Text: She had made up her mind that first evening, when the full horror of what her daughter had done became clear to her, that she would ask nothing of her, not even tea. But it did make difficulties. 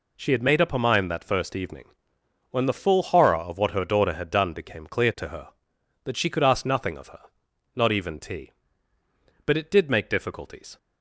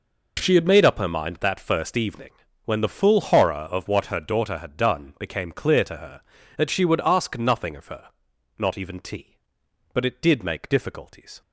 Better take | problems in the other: second | says "could" for "would"; at 6.2 s

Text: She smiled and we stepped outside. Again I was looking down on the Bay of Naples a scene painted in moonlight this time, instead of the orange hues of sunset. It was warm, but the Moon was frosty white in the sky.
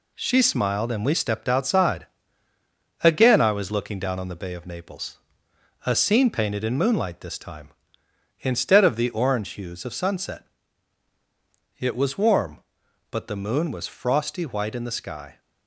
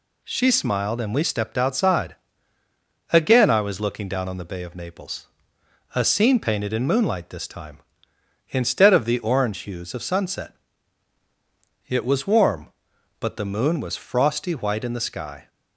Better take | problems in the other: second | gets quieter; throughout; 6 dB // pauses between "Naples" and "a"; noticeable; at 5.1 s; 0.68 s long; noticeable in the second

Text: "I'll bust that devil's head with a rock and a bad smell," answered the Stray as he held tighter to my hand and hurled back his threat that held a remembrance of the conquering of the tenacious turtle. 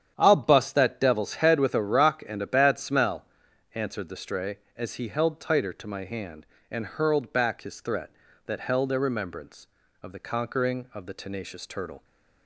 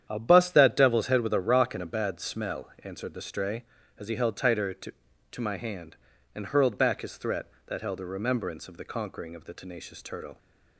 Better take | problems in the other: first | starts louder than the rest; strong; until 1.1 s; 9.5 dB; strong in the first // says "to" twice; at 5.3 s

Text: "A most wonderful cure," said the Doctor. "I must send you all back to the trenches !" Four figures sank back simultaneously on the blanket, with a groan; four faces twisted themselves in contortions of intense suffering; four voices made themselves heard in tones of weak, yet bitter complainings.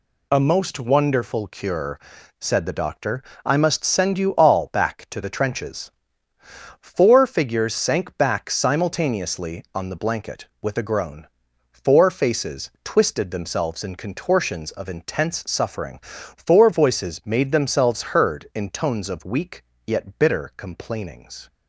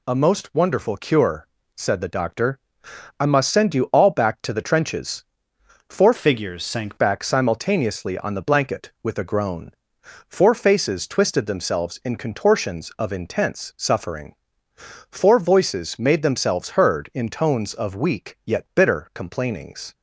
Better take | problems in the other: first | changes voice from "figures" to "sank"; from 6.1 to 6.9 s; 0.8 s long

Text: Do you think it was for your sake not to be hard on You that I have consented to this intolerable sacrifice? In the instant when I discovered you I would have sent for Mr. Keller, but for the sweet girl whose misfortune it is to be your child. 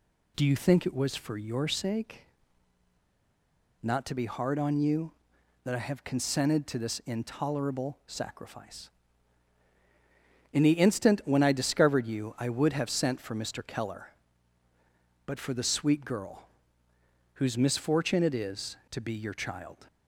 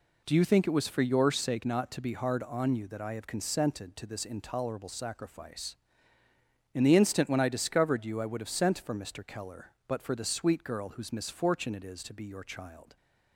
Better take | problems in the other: second | pauses between "sake" and "not"; strong; at 2.2 s; 1.5 s long // pauses between "girl" and "whose"; noticeable; at 16.4 s; 0.92 s long

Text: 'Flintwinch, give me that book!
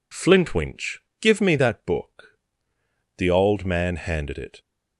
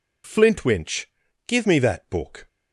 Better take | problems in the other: second | goes on to say "The old man handed it"; from 3.1 s on; 1.4 s long

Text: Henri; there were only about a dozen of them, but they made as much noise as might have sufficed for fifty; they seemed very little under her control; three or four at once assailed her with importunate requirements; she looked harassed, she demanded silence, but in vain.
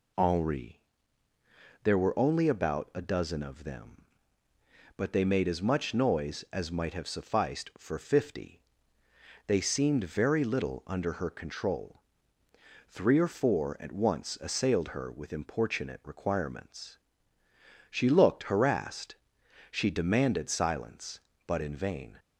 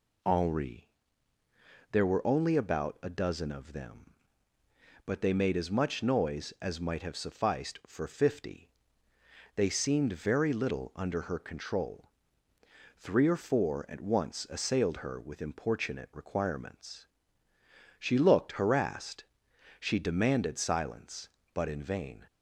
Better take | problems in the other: neither | none

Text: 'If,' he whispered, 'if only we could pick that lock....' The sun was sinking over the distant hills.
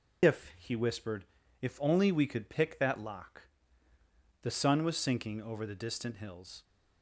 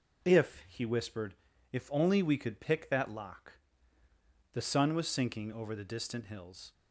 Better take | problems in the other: second | loses the start of "If"; at 0.2 s; 105 ms

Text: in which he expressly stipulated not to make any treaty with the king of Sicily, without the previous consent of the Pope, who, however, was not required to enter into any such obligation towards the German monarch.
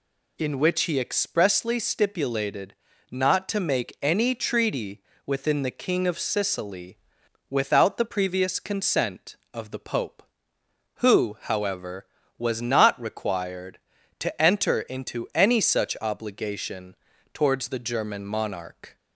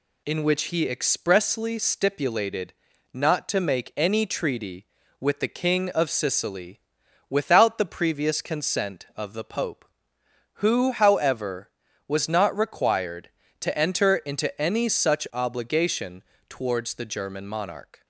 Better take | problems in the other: second | pauses between "stipulated" and "not"; slight; at 2.7 s; 0.36 s long; also in the second // says "within" for "with"; at 5.2 s // pauses between "obligation" and "towards"; at 16.9 s; 0.38 s long; slight in the second

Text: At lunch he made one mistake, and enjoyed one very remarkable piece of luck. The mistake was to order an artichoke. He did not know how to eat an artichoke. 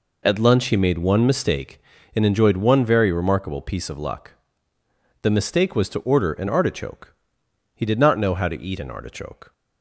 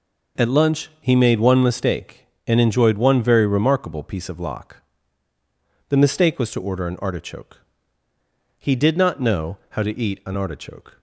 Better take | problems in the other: first | says "lock" for "luck"; at 4.3 s

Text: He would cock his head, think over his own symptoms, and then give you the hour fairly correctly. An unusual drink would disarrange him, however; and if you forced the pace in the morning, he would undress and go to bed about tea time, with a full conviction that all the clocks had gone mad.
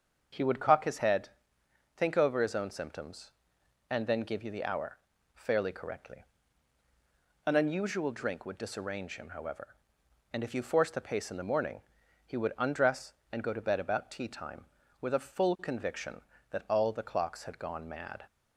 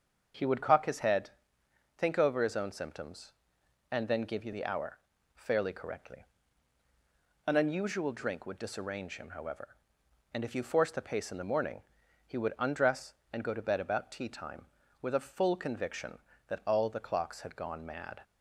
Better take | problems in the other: neither | starts louder than the rest; the same in both // pauses between "hour" and "fairly"; the same in both

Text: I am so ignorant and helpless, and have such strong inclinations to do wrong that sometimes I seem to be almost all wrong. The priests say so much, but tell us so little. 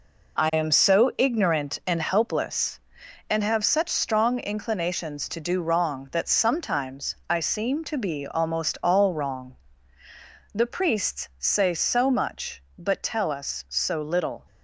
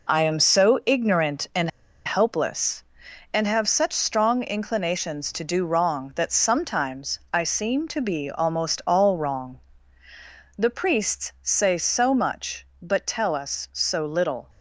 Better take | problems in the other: first | pauses between "and" and "helpless"; at 1.6 s; 0.37 s long

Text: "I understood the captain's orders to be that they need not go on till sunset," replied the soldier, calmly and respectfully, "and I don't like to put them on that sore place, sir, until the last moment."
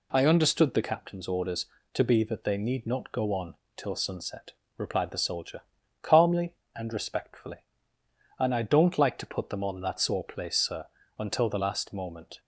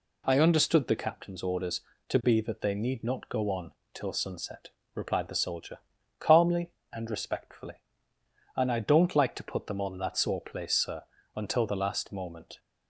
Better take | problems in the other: neither | pauses between "on" and "till"; slight; the same in both

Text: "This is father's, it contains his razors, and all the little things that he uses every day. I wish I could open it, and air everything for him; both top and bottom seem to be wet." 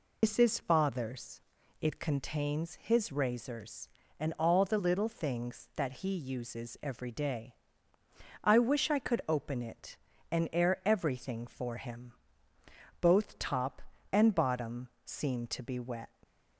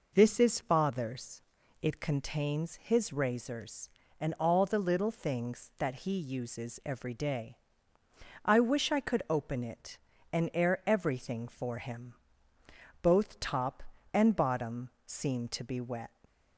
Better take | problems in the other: second | loses the start of "This"; at 0.2 s; 100 ms // pauses between "bottom" and "seem"; slight; at 14.8 s; 0.16 s long; slight in the second

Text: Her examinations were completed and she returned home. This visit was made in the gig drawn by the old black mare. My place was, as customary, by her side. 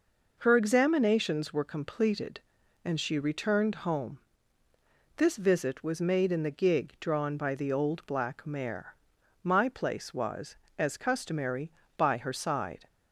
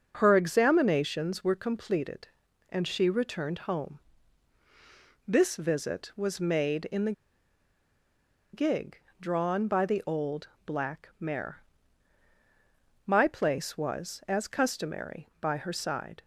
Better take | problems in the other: first | starts louder than the rest; noticeable; until 1.2 s; 6 dB // pauses between "the" and "gig"; strong; at 7.1 s; 1.4 s long // pauses between "gig" and "drawn"; slight; at 8.9 s; 0.22 s long // pauses between "old" and "black"; slight; at 10.4 s; 0.18 s long

